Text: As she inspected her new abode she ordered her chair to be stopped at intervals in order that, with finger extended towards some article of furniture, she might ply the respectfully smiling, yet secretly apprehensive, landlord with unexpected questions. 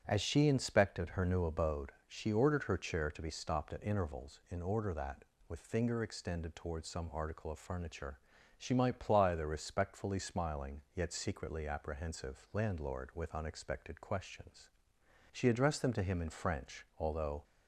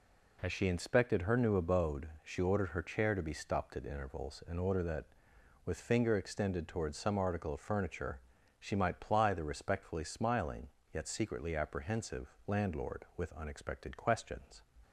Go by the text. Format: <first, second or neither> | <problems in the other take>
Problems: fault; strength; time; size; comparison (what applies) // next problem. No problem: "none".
second | starts louder than the rest; strong; until 1.0 s; 8.5 dB // pauses between "abode" and "she"; slight; at 1.9 s; 0.18 s long; slight in the second // goes on to say "She addressed them to him in French although"; strong; from 15.3 s on; 2.1 s long